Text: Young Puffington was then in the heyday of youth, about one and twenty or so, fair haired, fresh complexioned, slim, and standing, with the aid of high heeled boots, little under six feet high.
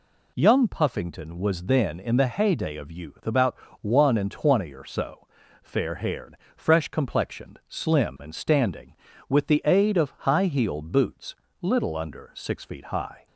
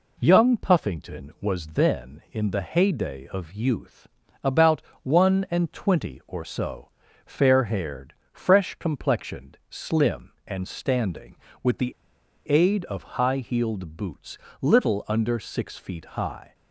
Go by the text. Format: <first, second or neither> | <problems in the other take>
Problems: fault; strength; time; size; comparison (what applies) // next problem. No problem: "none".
first | pauses between "about" and "one"; slight; at 4.8 s; 0.22 s long; slight in the first // pauses between "the" and "aid"; noticeable; at 11.9 s; 0.55 s long